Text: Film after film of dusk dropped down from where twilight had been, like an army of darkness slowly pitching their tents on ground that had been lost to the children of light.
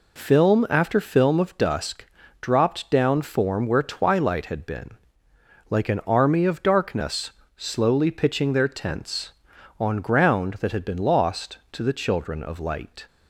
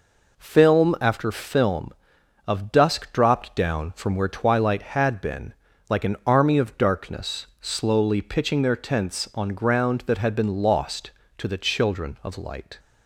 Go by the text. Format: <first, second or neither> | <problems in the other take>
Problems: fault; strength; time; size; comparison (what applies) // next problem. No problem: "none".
second | pauses between "dusk" and "dropped"; slight; at 2.0 s; 0.36 s long // says "form" for "from"; at 3.2 s // pauses between "darkness" and "slowly"; slight; at 7.3 s; 0.24 s long